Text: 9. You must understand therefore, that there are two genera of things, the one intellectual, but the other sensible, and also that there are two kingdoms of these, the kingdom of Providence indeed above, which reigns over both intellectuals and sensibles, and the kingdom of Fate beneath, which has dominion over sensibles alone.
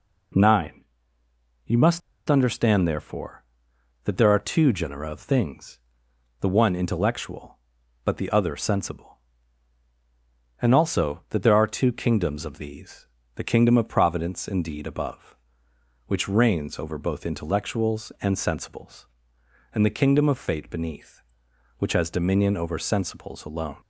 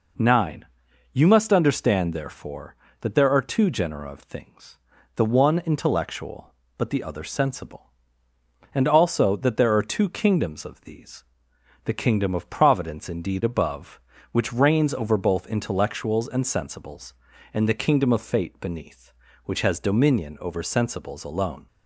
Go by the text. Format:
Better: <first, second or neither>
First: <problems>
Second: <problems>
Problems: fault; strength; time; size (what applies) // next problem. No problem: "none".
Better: second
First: pauses between "must" and "understand"; slight; at 2.0 s; 0.28 s long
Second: none